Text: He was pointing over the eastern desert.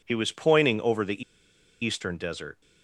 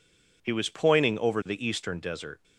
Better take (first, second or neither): second